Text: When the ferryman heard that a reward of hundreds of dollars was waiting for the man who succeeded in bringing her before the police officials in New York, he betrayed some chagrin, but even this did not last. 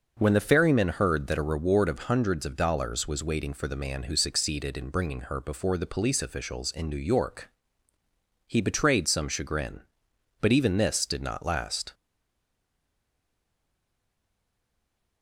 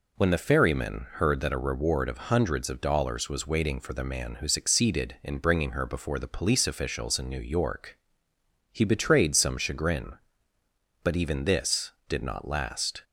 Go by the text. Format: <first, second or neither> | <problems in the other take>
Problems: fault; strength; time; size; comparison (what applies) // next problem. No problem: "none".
second | stays silent after the last word; strong; from 11.9 s on; 3.3 s long